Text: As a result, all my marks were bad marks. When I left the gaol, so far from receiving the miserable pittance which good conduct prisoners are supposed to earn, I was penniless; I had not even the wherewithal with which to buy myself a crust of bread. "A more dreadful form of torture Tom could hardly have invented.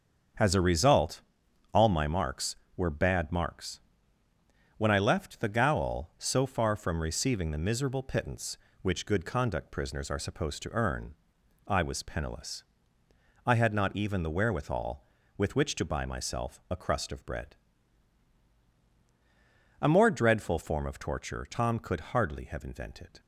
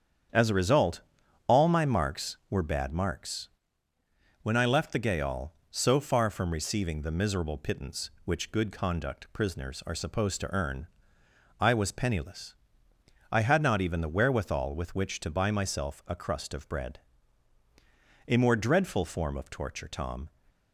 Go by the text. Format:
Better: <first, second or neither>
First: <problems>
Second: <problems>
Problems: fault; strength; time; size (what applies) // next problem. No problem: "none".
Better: first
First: starts louder than the rest; strong; until 1.8 s; 7 dB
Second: starts louder than the rest; strong; until 1.7 s; 8.5 dB // stops before "could hardly have invented"; at 20.4 s